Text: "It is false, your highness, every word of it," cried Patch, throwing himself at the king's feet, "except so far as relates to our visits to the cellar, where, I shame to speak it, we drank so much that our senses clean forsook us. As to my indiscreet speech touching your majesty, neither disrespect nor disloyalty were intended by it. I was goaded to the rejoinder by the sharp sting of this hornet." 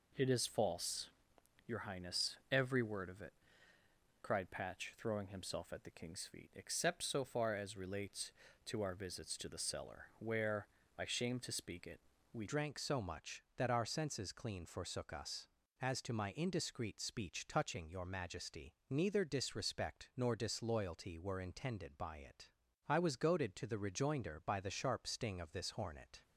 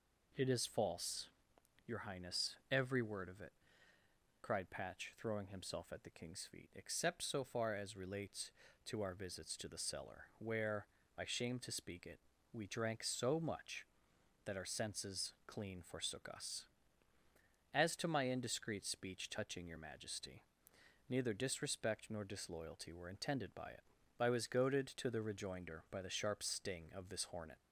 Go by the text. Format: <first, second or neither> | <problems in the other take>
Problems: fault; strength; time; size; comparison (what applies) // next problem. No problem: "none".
second | changes voice at "drank"; from 12.4 s on; 13.8 s long